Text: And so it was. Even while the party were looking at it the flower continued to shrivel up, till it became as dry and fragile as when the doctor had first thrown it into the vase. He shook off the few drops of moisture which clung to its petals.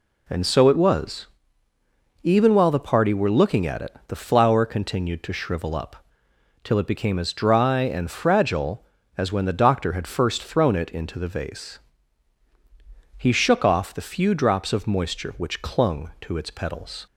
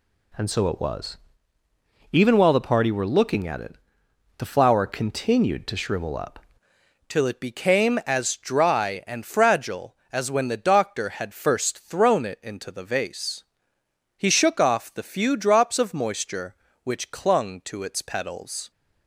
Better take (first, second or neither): first